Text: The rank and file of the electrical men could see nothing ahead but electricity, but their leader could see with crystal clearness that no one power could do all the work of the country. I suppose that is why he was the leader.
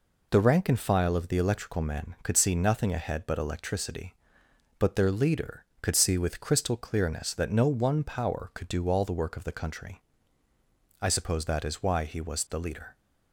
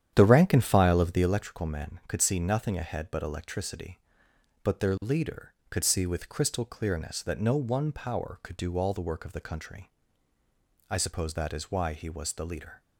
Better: first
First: none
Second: starts louder than the rest; strong; until 1.4 s; 9.5 dB

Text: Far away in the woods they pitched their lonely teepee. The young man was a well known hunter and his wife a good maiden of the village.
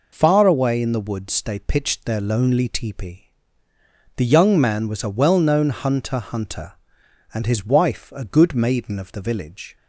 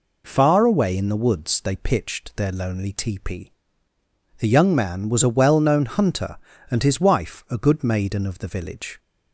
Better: second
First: says "hunter" twice; at 6.1 s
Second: none

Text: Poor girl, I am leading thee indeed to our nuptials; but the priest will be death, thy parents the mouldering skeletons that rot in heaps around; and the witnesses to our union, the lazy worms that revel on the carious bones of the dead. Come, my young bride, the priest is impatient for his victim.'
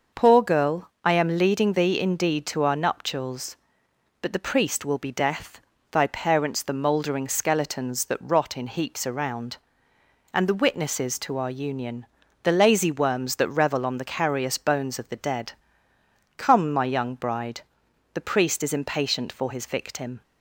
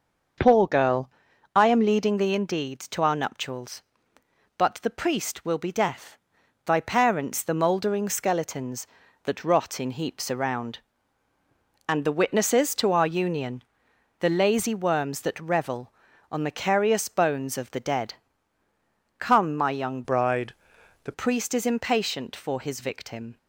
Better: first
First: starts louder than the rest; noticeable; until 1.2 s; 6 dB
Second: starts louder than the rest; until 1.8 s; 6.5 dB // changes voice from "bride" to "the"; from 20.0 to 21.1 s; 1.1 s long

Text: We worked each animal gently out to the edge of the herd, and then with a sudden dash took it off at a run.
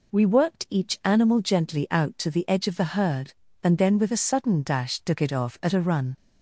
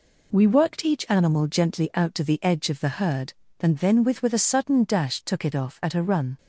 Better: first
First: none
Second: says "with" twice; at 4.2 s

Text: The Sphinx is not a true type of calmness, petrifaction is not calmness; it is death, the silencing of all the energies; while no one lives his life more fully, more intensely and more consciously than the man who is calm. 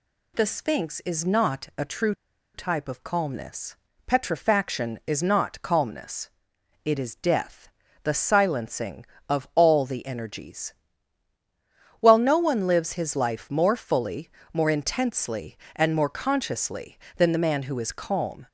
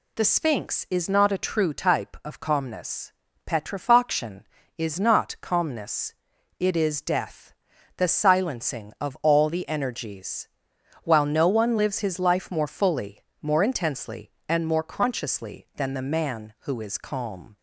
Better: second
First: pauses between "true" and "type"; at 2.1 s; 0.41 s long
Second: none

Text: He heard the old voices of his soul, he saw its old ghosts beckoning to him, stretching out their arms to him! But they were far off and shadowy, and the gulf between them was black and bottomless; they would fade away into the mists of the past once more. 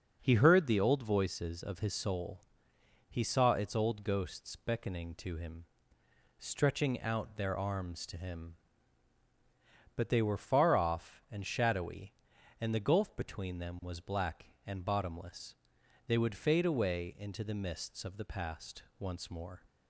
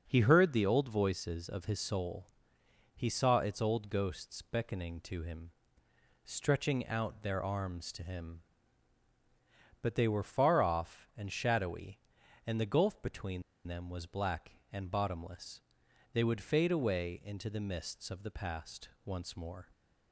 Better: first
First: starts louder than the rest; noticeable; until 1.2 s; 6 dB // pauses between "past" and "once"; slight; at 18.8 s; 0.16 s long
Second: starts louder than the rest; noticeable; until 1.0 s; 6 dB // pauses between "between" and "them"; slight; at 13.4 s; 0.23 s long // pauses between "past" and "once"; slight; at 18.9 s; 0.16 s long

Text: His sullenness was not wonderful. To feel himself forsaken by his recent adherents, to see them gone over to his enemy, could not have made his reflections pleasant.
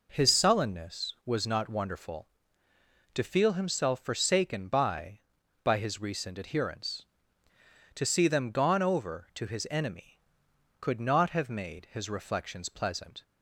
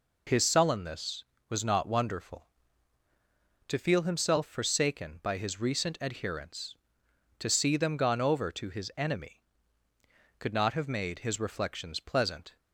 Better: second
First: says "by" twice; at 5.6 s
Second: none

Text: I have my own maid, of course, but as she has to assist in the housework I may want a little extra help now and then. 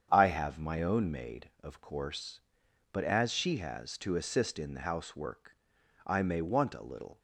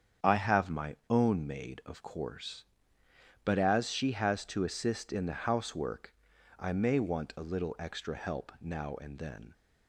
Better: second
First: starts louder than the rest; strong; until 1.1 s; 8 dB // pauses between "housework" and "I"; noticeable; at 5.5 s; 0.50 s long // stops before "extra help now and then"; at 7.1 s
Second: starts louder than the rest; strong; until 1.3 s; 8 dB // pauses between "housework" and "I"; noticeable; at 6.1 s; 0.46 s long

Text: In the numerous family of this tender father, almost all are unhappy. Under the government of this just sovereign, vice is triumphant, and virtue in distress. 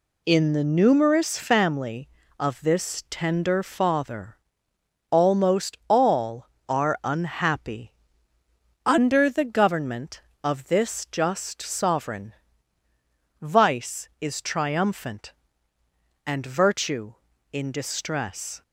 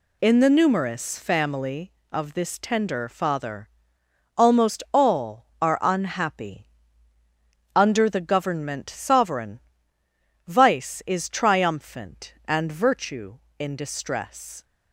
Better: first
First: none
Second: skips "of this just"; at 8.8 s

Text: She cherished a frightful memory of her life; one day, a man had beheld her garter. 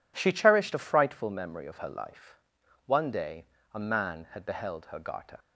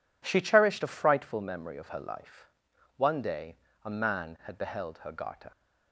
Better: neither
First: none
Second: none

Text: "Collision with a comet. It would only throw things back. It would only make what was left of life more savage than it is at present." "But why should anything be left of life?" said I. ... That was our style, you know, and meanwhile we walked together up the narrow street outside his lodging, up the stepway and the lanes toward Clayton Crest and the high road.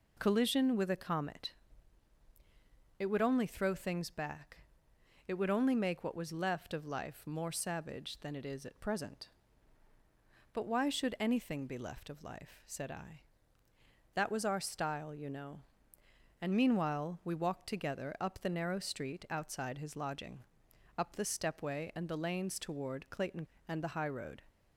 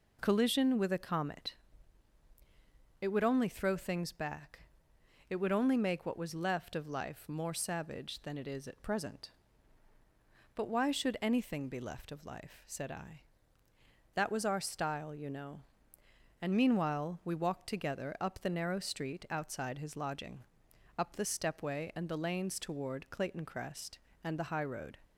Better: second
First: skips "Crest"; at 23.5 s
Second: none

